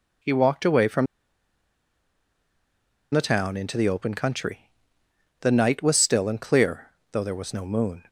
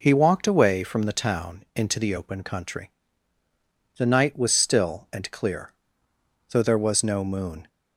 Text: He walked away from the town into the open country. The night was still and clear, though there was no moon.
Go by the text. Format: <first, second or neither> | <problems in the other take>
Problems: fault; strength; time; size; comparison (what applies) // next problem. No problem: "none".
second | pauses between "from" and "the"; strong; at 1.0 s; 2.0 s long